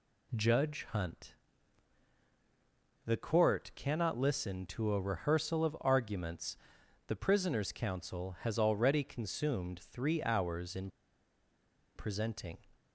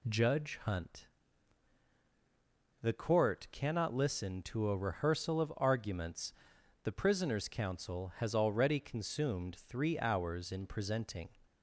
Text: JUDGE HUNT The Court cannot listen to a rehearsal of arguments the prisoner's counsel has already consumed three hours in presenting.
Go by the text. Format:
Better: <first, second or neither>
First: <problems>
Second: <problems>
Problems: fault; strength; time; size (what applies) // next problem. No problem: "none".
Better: second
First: pauses between "HUNT" and "The"; strong; at 1.3 s; 1.7 s long // pauses between "arguments" and "the"; noticeable; at 6.5 s; 0.52 s long // pauses between "in" and "presenting"; at 10.8 s; 1.0 s long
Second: pauses between "HUNT" and "The"; strong; at 1.0 s; 1.7 s long // pauses between "arguments" and "the"; noticeable; at 6.3 s; 0.52 s long